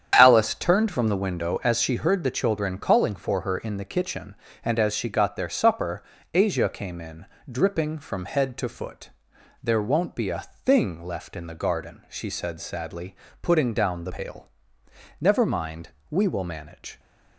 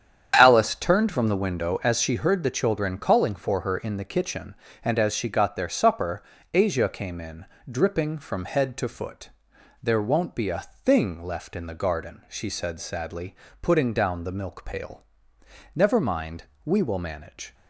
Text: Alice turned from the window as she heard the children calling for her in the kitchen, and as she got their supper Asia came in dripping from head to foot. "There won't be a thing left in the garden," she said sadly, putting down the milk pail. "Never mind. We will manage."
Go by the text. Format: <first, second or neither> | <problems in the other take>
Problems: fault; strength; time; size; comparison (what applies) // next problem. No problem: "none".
second | starts louder than the rest; strong; until 1.1 s; 8.5 dB; strong in the second // pauses between "supper" and "Asia"; slight; at 6.0 s; 0.28 s long; slight in the second // pauses between "in" and "dripping"; slight; at 7.2 s; 0.24 s long; slight in the second // skips "milk"; at 14.1 s